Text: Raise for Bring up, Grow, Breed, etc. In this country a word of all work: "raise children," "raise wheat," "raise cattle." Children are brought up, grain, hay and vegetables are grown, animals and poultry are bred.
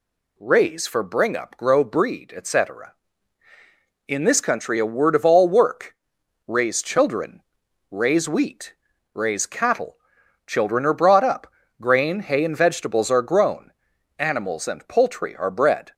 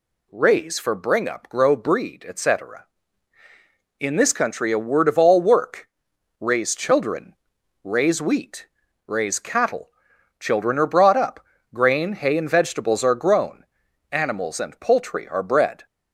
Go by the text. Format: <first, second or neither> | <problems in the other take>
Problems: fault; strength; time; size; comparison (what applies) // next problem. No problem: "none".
neither | none